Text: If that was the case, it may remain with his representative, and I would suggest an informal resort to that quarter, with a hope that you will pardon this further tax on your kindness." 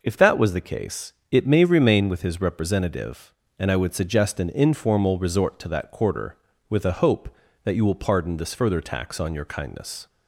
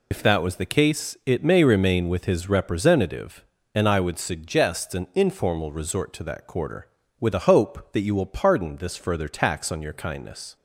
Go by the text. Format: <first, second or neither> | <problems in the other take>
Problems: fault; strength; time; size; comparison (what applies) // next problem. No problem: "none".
first | loses the start of "If"; at 0.1 s; 65 ms